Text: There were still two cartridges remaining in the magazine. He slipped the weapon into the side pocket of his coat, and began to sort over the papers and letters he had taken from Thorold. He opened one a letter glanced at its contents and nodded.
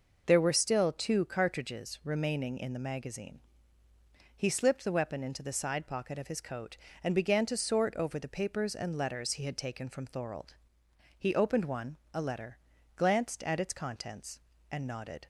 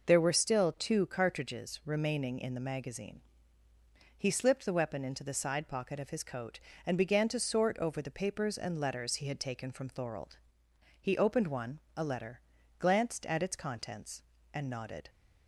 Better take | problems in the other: neither | pauses between "one" and "a"; slight; the same in both // pauses between "letter" and "glanced"; the same in both

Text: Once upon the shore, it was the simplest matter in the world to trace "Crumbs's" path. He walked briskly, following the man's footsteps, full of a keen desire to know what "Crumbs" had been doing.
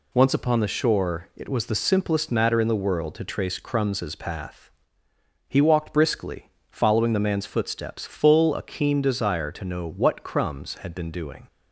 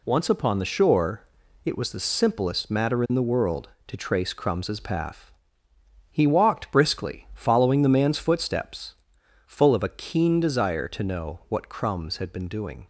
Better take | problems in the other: second | skips "of"; at 8.5 s

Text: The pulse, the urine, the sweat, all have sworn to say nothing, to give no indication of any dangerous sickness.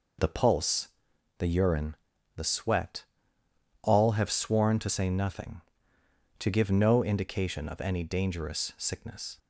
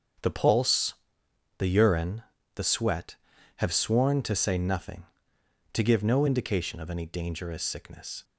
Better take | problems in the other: first | starts louder than the rest; strong; until 1.8 s; 7.5 dB // skips "all"; at 3.3 s

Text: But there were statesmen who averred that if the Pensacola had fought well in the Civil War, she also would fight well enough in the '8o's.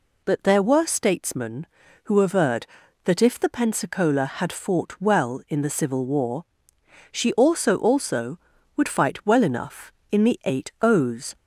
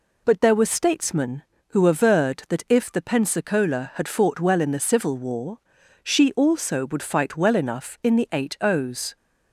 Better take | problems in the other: second | says "also" twice; at 7.7 s

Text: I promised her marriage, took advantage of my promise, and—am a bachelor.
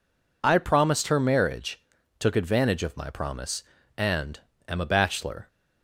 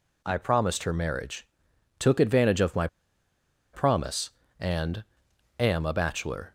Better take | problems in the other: first | pauses between "my" and "promise"; noticeable; at 2.8 s; 0.86 s long

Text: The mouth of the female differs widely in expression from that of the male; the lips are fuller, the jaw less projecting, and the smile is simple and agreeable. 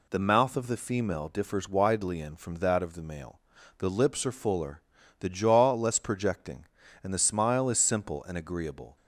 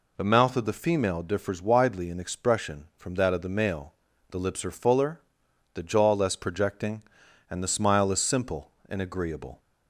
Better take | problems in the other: second | skips "expression"; at 2.3 s

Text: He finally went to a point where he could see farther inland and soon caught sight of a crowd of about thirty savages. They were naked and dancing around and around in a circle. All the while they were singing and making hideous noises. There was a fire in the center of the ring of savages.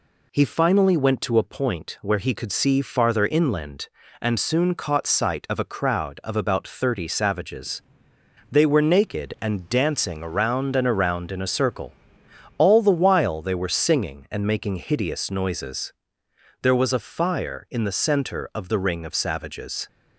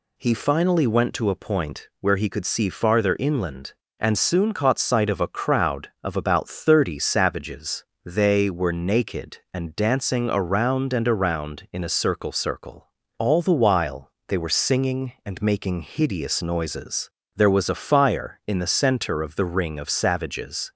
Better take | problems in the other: first | says "circle" twice; at 12.3 s // pauses between "while" and "they"; slight; at 14.1 s; 0.16 s long

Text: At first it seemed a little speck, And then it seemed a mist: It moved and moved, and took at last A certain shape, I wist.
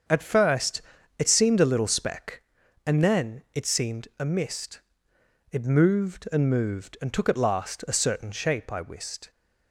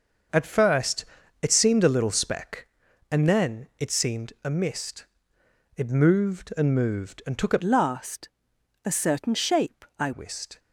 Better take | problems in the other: first | starts louder than the rest; until 1.6 s; 6 dB; also in the first // pauses between "first" and "it"; slight; at 1.0 s; 0.36 s long; slight in the first // changes voice from "last" to "I"; from 7.6 to 10.1 s; 2.5 s long // pauses between "last" and "A"; noticeable; at 8.2 s; 0.56 s long

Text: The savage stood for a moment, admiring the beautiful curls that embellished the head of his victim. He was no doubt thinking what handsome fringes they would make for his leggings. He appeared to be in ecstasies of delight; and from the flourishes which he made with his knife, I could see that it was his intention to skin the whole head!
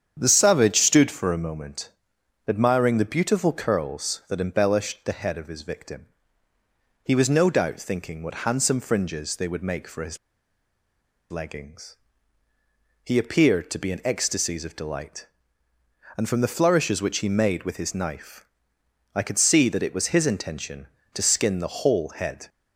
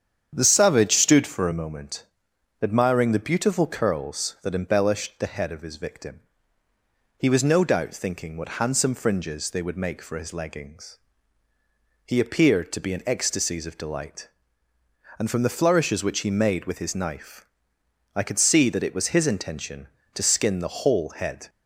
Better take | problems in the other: second | starts louder than the rest; strong; until 1.2 s; 8.5 dB; strong in the second // pauses between "his" and "leggings"; at 10.1 s; 1.1 s long

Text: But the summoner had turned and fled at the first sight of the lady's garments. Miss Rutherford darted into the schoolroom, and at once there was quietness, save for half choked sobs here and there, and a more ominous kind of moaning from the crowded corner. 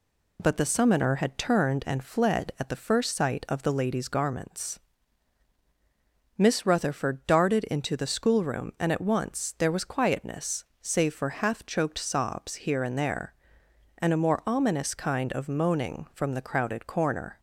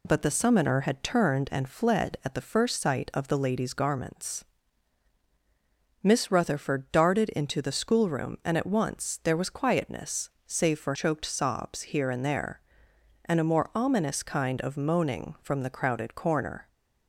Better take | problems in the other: first | skips "half"; at 10.9 s

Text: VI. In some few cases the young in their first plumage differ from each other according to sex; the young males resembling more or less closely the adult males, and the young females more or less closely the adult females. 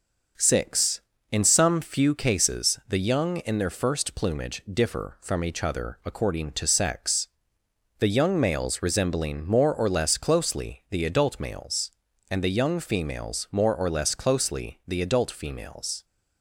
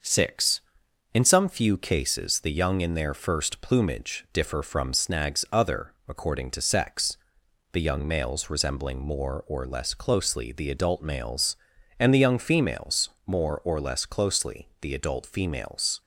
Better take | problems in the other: first | starts louder than the rest; noticeable; until 1.5 s; 6 dB // says "snags" for "each"; at 4.9 s // pauses between "other" and "according"; slight; at 5.9 s; 0.16 s long // pauses between "females" and "more"; slight; at 13.1 s; 0.16 s long

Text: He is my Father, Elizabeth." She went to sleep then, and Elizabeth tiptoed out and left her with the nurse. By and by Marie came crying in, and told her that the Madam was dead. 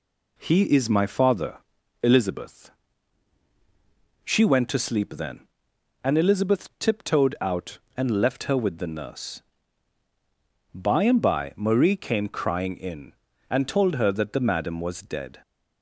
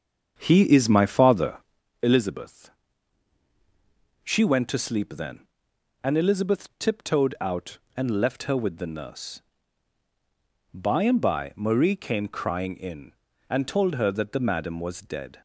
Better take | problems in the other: first | starts louder than the rest; strong; until 1.8 s; 7 dB

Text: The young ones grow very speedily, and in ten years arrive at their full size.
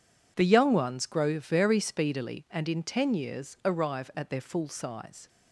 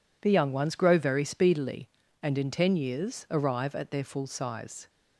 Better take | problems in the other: neither | none

